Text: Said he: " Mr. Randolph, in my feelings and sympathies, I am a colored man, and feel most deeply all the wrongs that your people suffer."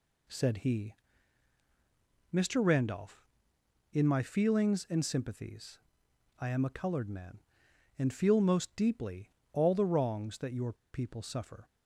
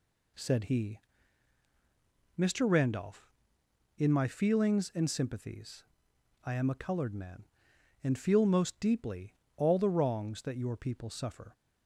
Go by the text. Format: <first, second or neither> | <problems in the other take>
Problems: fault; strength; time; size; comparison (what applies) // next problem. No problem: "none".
second | pauses between "deeply" and "all"; slight; at 9.2 s; 0.24 s long; slight in the second // pauses between "your" and "people"; slight; at 10.7 s; 0.19 s long